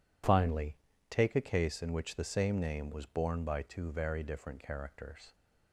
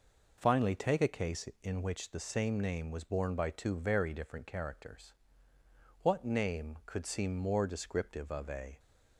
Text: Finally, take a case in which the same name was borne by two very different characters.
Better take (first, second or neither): first